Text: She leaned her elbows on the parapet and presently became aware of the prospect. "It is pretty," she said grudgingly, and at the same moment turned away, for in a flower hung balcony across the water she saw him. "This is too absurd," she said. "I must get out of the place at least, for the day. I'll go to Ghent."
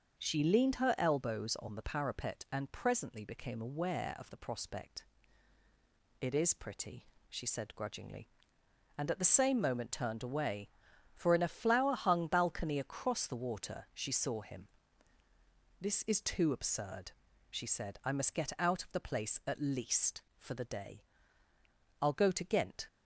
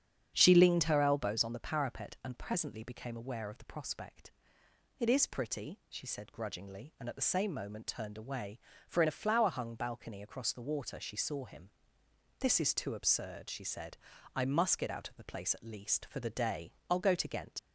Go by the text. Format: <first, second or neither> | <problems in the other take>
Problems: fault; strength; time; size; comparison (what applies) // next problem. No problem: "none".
first | starts louder than the rest; strong; until 1.3 s; 8 dB; also in the first // leaves "Ghent" unfinished; at 17.5 s; 75 ms